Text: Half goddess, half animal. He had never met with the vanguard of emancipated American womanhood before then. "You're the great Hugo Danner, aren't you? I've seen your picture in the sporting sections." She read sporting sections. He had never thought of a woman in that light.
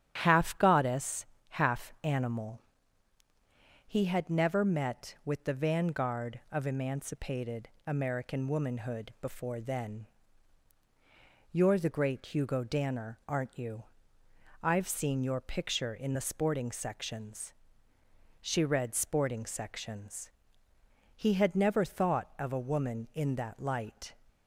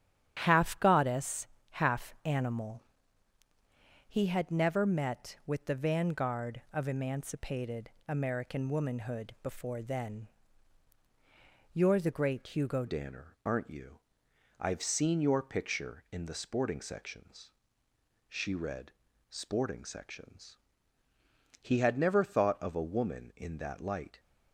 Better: first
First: starts louder than the rest; strong; until 1.2 s; 10 dB // pauses between "emancipated" and "American"; slight; at 7.6 s; 0.18 s long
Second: starts louder than the rest; strong; until 1.4 s; 10 dB // pauses between "emancipated" and "American"; slight; at 7.8 s; 0.18 s long // changes voice at "Danner"; from 12.8 s on; 11.3 s long // pauses between "read" and "sporting"; slight; at 18.9 s; 0.36 s long

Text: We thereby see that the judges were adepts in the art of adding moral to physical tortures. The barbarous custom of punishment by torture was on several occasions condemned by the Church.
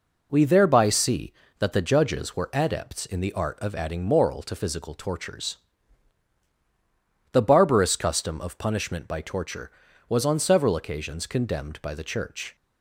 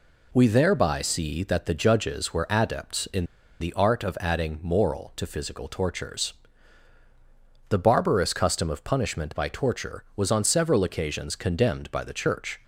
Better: first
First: none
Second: pauses between "in" and "the"; slight; at 3.2 s; 0.35 s long

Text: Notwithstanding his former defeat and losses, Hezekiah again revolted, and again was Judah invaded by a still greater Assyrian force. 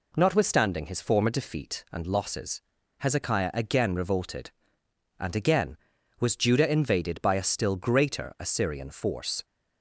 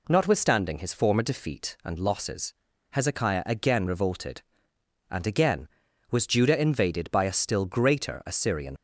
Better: first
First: none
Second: stops before "force"; at 8.7 s

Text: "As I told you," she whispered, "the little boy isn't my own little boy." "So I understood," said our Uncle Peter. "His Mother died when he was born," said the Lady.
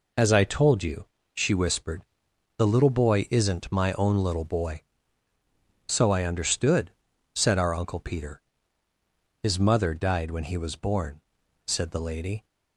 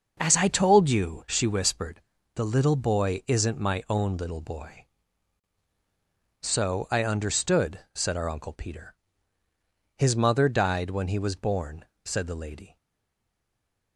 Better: first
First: none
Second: starts louder than the rest; until 1.2 s; 6 dB // stays silent after the last word; noticeable; from 12.7 s on; 1.2 s long

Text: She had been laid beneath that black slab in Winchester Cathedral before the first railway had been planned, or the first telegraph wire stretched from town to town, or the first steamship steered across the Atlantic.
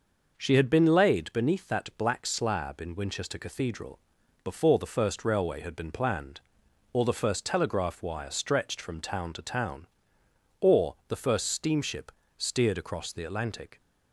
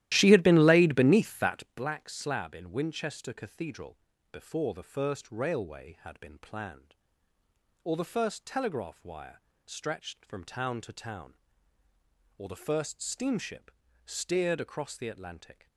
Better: first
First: pauses between "Cathedral" and "before"; at 3.9 s; 0.44 s long // pauses between "steamship" and "steered"; slight; at 12.1 s; 0.26 s long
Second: starts louder than the rest; strong; until 1.8 s; 14.5 dB // pauses between "Cathedral" and "before"; slight; at 3.9 s; 0.34 s long // pauses between "wire" and "stretched"; slight; at 9.4 s; 0.24 s long // pauses between "steamship" and "steered"; slight; at 13.7 s; 0.34 s long

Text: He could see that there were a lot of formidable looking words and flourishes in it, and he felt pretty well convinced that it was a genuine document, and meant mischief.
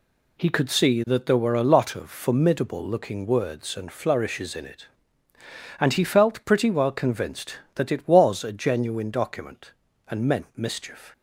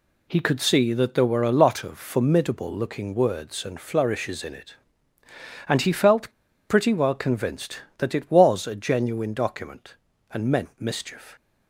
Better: first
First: none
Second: pauses between "felt" and "pretty"; at 6.3 s; 0.37 s long

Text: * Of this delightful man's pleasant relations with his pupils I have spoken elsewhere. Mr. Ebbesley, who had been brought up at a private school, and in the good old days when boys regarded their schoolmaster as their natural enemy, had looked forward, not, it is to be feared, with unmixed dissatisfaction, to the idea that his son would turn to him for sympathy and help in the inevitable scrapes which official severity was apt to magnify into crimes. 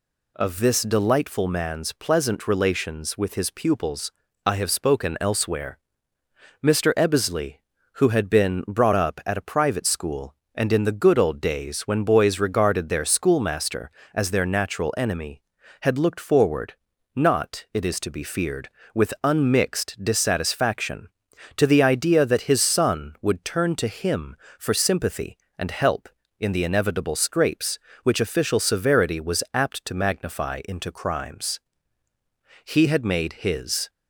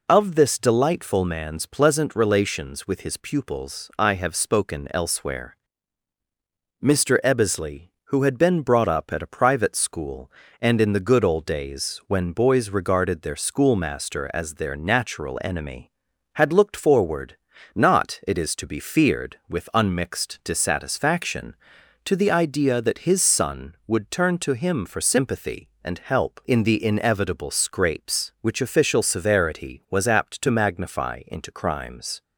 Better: second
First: pauses between "pupils" and "I"; slight; at 4.1 s; 0.34 s long // goes on to say "He had made his"; noticeable; from 32.6 s on; 1.2 s long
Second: none

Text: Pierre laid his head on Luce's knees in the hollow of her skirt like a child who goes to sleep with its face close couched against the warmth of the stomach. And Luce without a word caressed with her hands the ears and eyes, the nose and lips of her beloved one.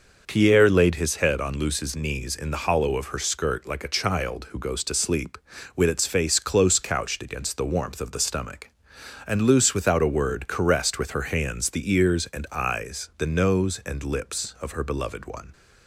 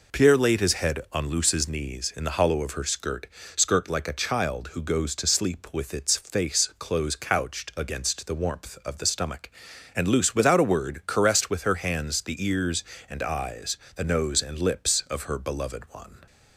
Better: first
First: none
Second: says "skirt" twice; at 3.5 s

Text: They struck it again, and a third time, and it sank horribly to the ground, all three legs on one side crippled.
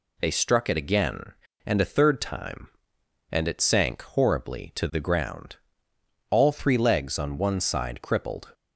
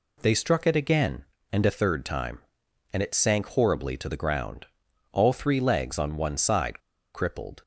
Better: first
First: none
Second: pauses between "side" and "crippled"; slight; at 6.8 s; 0.33 s long

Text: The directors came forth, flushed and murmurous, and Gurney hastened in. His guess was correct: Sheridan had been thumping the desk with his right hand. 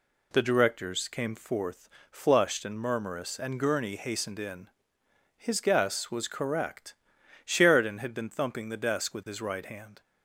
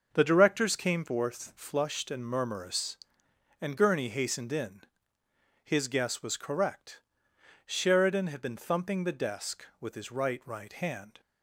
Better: first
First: none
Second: says "right" twice; at 10.4 s

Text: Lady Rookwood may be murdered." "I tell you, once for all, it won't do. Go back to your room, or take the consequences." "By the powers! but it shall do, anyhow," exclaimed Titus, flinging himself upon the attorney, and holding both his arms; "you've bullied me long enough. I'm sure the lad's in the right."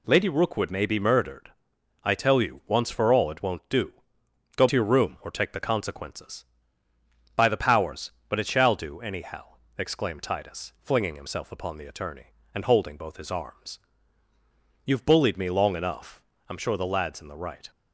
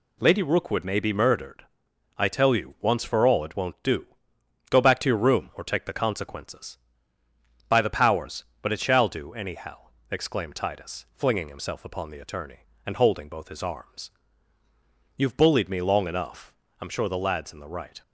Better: second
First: skips "back"; at 4.6 s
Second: none

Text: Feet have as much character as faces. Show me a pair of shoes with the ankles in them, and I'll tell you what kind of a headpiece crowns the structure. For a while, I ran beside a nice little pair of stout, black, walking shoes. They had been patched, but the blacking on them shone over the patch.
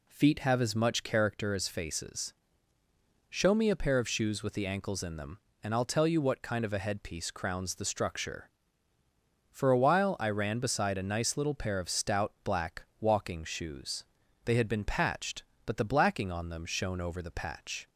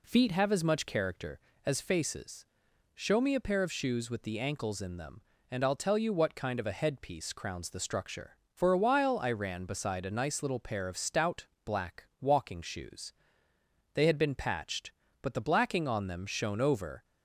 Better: first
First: none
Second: stops before "the patch"; at 17.0 s

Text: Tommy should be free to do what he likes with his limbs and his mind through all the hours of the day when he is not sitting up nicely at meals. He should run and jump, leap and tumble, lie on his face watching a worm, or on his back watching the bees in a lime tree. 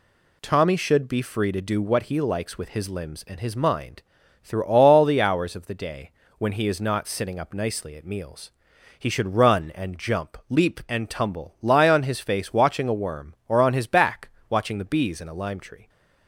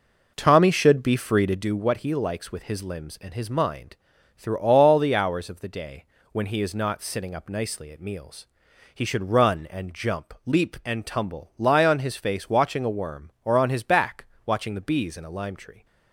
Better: first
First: pauses between "mind" and "through"; at 4.0 s; 0.42 s long // pauses between "day" and "when"; slight; at 6.1 s; 0.26 s long // pauses between "back" and "watching"; slight; at 14.2 s; 0.20 s long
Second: starts louder than the rest; noticeable; until 1.6 s; 5 dB // pauses between "mind" and "through"; at 3.9 s; 0.42 s long // pauses between "day" and "when"; slight; at 6.0 s; 0.26 s long // pauses between "back" and "watching"; slight; at 14.2 s; 0.20 s long

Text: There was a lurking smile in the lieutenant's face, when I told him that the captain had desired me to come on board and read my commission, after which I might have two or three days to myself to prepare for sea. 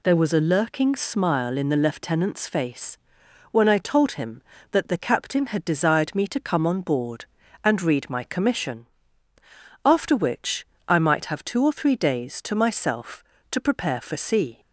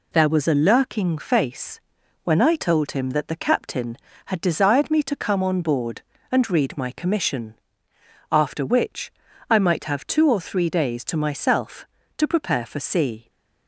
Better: first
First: pauses between "which" and "I"; slight; at 10.6 s; 0.22 s long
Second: skips "smile in the lieutenant's"; at 1.1 s // pauses between "which" and "I"; at 9.1 s; 0.38 s long

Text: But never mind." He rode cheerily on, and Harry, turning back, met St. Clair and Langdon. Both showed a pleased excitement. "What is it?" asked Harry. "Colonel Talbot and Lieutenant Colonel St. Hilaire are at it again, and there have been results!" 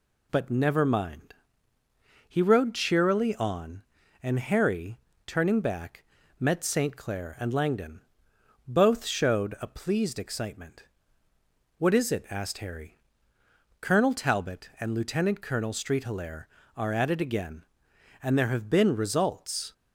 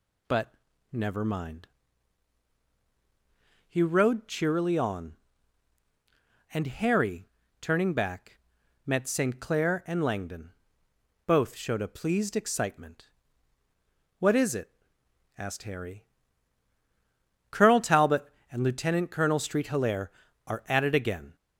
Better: first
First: none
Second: pauses between "But" and "never"; at 0.5 s; 0.38 s long // stops before "and there have been results"; at 21.3 s

